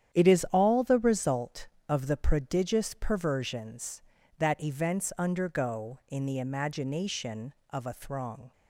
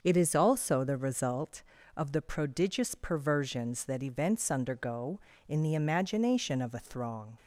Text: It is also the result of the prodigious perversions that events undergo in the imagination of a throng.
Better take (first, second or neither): second